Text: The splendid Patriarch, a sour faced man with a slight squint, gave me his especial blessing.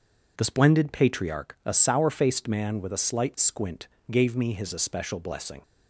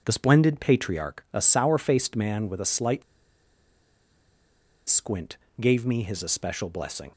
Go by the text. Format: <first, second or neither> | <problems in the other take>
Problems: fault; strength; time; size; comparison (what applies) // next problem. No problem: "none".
first | pauses between "slight" and "squint"; strong; at 3.0 s; 1.8 s long